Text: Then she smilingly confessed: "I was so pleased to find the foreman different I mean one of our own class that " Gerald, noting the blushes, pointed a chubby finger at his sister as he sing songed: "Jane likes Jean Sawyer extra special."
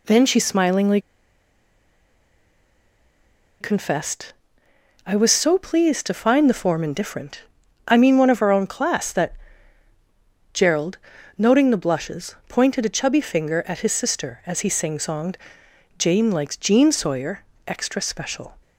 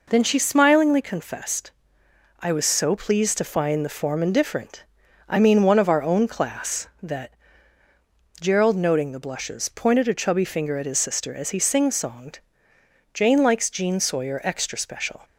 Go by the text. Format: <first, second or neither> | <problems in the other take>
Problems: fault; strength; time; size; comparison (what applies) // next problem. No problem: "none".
second | pauses between "smilingly" and "confessed"; strong; at 0.9 s; 2.6 s long // pauses between "different" and "I"; noticeable; at 7.4 s; 0.46 s long; also in the second // pauses between "Sawyer" and "extra"; slight; at 17.4 s; 0.24 s long